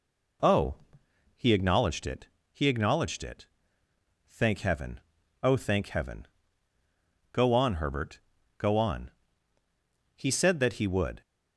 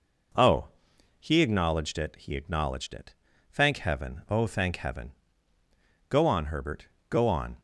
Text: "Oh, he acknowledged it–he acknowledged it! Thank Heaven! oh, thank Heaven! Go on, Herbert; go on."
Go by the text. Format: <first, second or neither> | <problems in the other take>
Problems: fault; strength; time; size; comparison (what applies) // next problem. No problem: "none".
second | goes on to say "He said that he would"; noticeable; from 10.1 s on; 1.0 s long